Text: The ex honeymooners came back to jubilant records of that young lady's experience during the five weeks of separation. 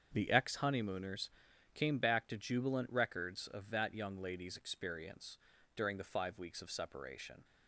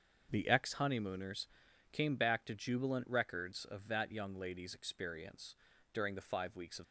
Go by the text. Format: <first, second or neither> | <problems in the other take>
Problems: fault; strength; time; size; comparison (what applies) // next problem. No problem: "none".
first | starts louder than the rest; until 1.3 s; 6.5 dB; strong in the first // pauses between "honeymooners" and "came"; at 1.4 s; 0.42 s long; also in the first // pauses between "experience" and "during"; slight; at 5.5 s; 0.36 s long; slight in the first // stops before "separation"; at 6.8 s